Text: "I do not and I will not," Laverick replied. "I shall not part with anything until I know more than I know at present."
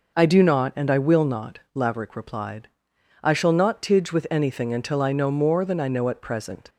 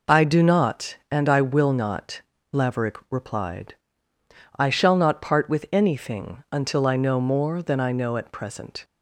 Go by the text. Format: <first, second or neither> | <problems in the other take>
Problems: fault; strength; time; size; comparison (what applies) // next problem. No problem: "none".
second | says "tidge" for "part"; at 3.8 s